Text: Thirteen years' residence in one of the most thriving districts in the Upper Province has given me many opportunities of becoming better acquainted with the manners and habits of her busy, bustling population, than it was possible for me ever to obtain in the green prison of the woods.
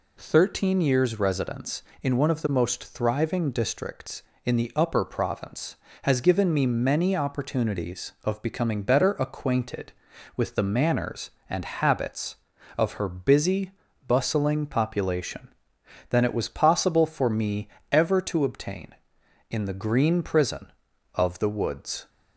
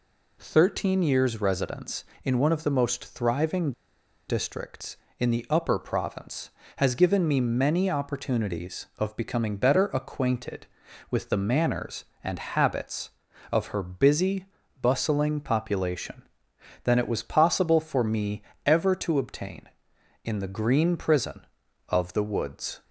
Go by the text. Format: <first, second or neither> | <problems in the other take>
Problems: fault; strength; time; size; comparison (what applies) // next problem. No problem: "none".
first | pauses between "thriving" and "districts"; noticeable; at 3.7 s; 0.56 s long // pauses between "me" and "ever"; slight; at 18.4 s; 0.24 s long; slight in the first